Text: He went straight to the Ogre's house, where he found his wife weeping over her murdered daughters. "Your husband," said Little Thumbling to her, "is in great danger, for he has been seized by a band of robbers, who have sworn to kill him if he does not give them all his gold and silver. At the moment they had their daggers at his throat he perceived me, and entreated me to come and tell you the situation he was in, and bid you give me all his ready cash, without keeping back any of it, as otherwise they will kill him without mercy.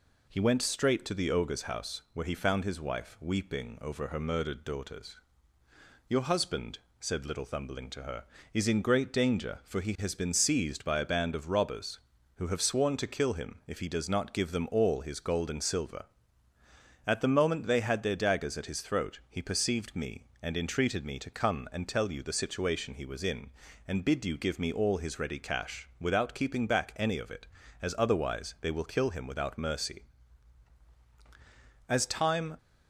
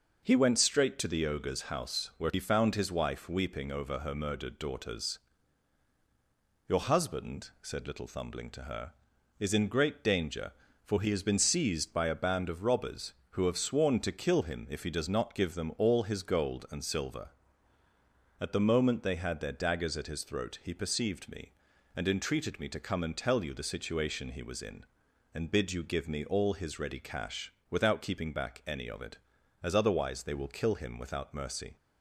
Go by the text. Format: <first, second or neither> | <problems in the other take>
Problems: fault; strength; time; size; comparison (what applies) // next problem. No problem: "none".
second | goes on to say "As time"; noticeable; from 31.8 s on; 0.68 s long